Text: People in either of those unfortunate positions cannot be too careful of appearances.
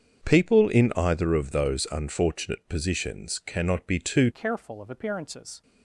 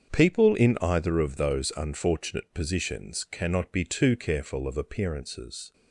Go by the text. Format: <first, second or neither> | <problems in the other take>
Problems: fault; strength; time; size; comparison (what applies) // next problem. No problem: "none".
second | starts louder than the rest; strong; until 1.2 s; 7.5 dB; strong in the second // changes voice at "careful"; from 4.3 s on; 1.3 s long